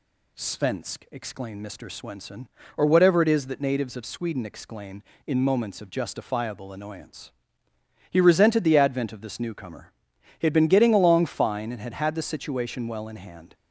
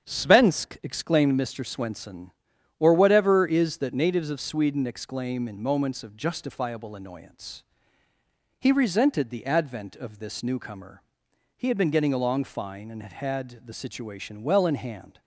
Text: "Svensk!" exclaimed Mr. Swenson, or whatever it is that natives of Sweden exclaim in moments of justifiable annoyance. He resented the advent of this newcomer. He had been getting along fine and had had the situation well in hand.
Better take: first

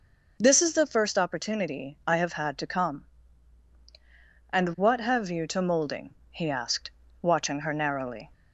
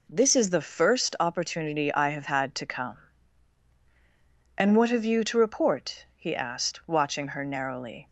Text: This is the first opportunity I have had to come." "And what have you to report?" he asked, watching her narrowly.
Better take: second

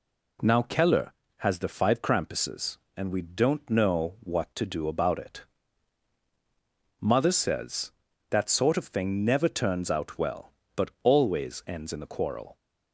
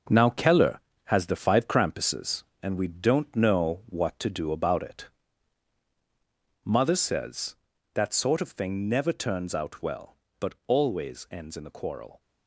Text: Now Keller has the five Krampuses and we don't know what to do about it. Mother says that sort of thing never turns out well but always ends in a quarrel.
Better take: first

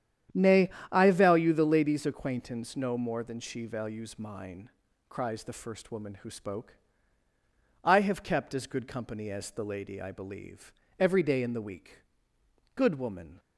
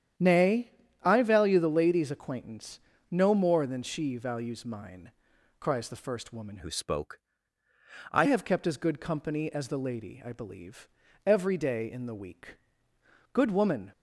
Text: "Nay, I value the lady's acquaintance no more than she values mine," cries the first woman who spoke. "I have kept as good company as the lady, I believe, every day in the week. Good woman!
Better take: first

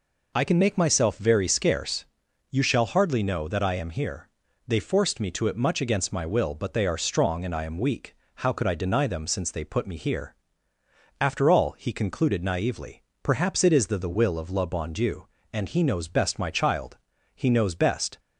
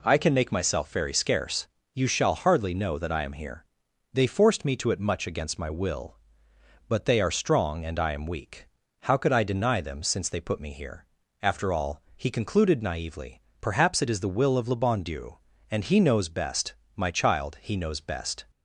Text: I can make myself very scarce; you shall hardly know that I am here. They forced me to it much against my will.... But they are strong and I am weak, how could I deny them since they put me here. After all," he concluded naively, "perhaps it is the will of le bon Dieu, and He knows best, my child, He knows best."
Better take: second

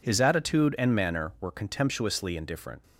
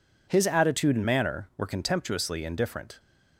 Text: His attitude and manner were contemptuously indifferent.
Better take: neither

